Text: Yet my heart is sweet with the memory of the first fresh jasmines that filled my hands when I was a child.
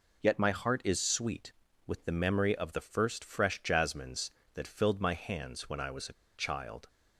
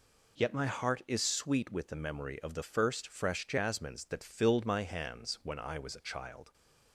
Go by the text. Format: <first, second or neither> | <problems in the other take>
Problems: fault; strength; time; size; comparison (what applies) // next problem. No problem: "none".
second | pauses between "a" and "child"; slight; at 6.1 s; 0.21 s long